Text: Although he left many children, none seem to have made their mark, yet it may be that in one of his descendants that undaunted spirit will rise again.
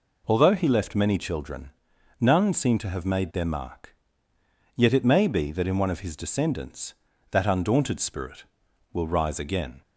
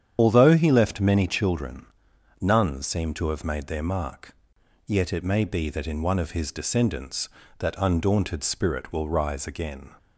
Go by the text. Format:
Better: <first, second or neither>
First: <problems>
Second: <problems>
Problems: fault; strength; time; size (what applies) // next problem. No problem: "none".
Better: first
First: none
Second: loses the start of "Although"; at 0.1 s; 35 ms // starts louder than the rest; strong; until 1.1 s; 8.5 dB